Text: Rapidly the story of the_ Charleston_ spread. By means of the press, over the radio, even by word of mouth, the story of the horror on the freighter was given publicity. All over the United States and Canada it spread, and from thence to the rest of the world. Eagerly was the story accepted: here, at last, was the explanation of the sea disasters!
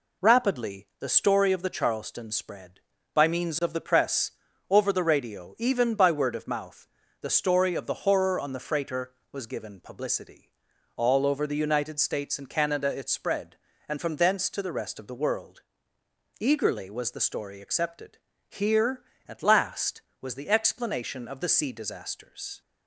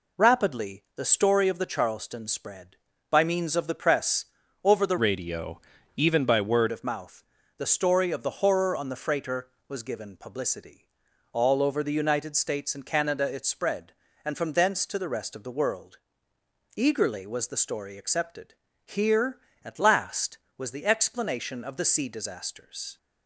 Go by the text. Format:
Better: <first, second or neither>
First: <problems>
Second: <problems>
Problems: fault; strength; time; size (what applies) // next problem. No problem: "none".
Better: first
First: none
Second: changes voice from "radio" to "word"; from 4.9 to 6.6 s; 1.7 s long